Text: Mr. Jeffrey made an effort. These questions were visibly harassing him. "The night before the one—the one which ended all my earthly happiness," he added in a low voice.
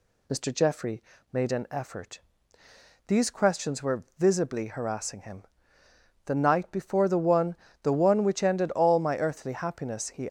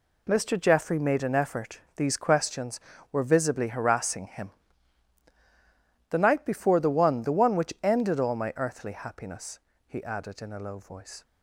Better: second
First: pauses between "Jeffrey" and "made"; slight; at 1.0 s; 0.30 s long // stops before "added in a low voice"; at 10.2 s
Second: none

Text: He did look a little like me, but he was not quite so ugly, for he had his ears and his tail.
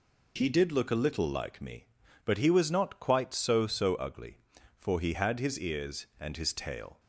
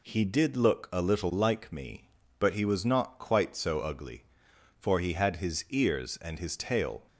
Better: second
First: says "so" twice; at 3.6 s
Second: none

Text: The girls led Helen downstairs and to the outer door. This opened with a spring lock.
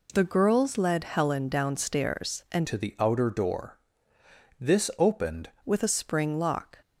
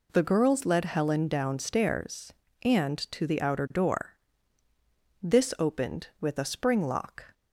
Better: second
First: changes voice from "to" to "opened"; from 2.6 to 5.4 s; 2.8 s long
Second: none

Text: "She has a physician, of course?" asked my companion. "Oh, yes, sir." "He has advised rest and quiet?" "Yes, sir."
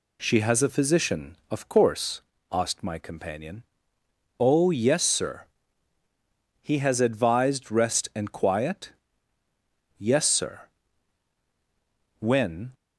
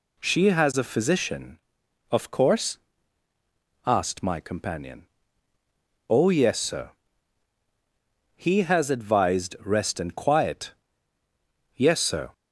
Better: second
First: goes on to say "When"; from 12.1 s on; 0.54 s long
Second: none

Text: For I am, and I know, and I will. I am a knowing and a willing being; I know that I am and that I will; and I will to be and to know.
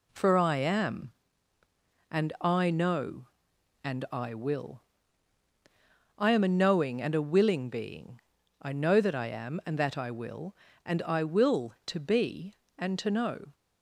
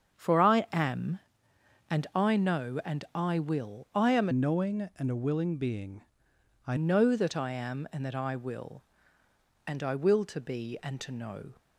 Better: first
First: none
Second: starts louder than the rest; strong; until 1.9 s; 7.5 dB // changes voice from "knowing" to "I"; from 4.3 to 6.7 s; 2.4 s long

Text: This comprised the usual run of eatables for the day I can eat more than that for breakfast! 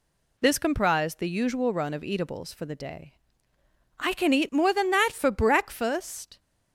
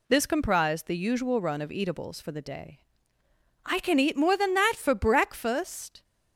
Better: neither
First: pauses between "day" and "I"; noticeable; at 3.1 s; 0.86 s long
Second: pauses between "day" and "I"; noticeable; at 2.7 s; 0.86 s long

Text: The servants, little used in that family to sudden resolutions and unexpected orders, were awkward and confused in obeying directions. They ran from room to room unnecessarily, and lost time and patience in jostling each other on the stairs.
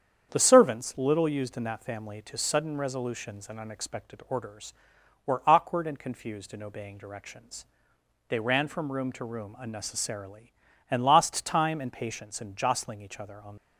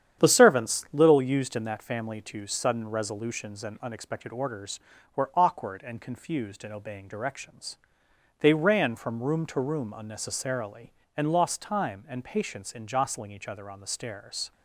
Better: second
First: starts louder than the rest; strong; until 1.3 s; 8 dB // stops before "the stairs"; at 13.5 s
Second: starts louder than the rest; strong; until 1.2 s; 9 dB

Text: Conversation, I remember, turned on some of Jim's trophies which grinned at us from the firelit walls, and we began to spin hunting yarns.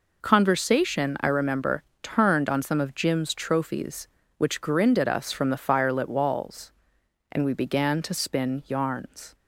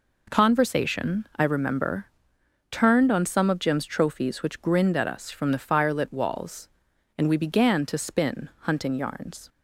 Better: second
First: skips "hunting"; at 8.6 s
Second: none

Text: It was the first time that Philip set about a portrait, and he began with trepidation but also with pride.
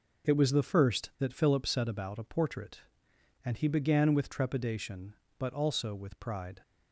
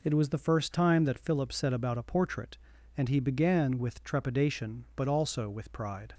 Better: second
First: skips "time"; at 1.1 s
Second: none

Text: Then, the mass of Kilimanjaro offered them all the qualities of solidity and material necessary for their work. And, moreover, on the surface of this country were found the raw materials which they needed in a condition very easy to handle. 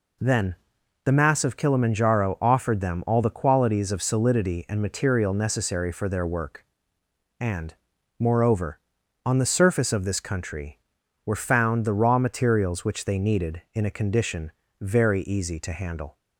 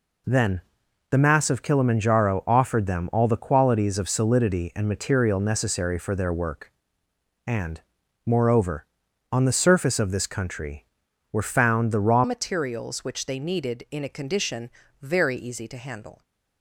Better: first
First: pauses between "condition" and "very"; slight; at 14.5 s; 0.30 s long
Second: changes voice at "materials"; from 12.2 s on; 4.0 s long // pauses between "condition" and "very"; slight; at 14.6 s; 0.32 s long

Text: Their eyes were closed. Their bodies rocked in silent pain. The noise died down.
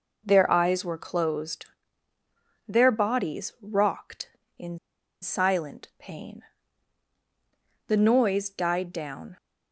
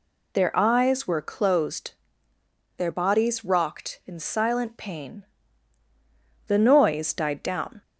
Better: second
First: pauses between "in" and "silent"; at 4.7 s; 0.43 s long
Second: none

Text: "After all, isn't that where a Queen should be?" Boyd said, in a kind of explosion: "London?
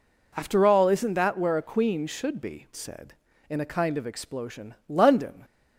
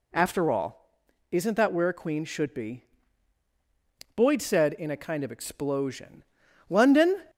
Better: second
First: skips "Boyd"; at 2.7 s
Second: none

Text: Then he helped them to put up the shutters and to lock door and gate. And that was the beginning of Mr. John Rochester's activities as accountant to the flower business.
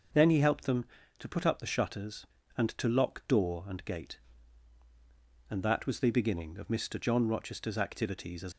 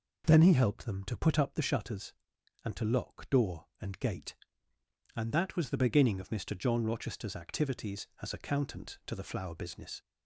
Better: second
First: stops before "accountant to the flower business"; at 8.5 s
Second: none

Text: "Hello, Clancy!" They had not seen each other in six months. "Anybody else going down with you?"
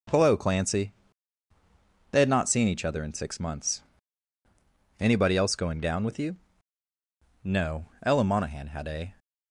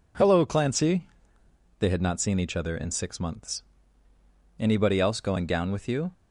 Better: second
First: goes on to say "No Ella Monahan had a"; strong; from 7.4 s on; 1.6 s long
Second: none

